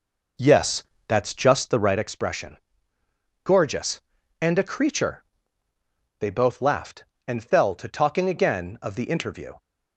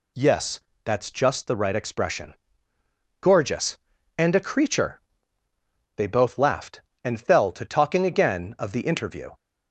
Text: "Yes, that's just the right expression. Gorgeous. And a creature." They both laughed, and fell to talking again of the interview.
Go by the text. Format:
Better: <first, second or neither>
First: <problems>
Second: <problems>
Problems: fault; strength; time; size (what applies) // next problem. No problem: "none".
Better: second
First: starts louder than the rest; noticeable; until 2.0 s; 5 dB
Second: none